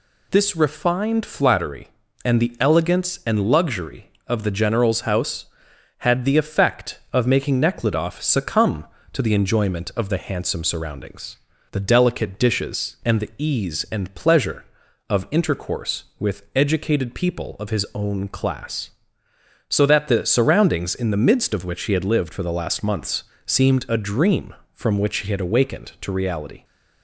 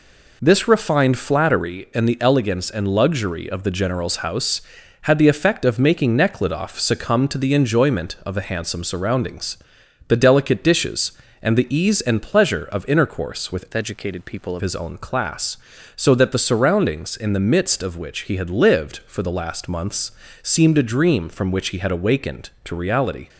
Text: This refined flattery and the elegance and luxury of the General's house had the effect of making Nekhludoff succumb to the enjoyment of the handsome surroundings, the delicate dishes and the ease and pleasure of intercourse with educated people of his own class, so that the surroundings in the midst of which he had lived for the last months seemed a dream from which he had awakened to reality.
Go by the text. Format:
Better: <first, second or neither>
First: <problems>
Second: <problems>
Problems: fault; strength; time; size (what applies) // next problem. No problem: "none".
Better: first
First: pauses between "months" and "seemed"; slight; at 23.2 s; 0.22 s long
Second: changes voice from "educated" to "of"; from 13.7 to 14.6 s; 0.9 s long // pauses between "months" and "seemed"; slight; at 20.1 s; 0.32 s long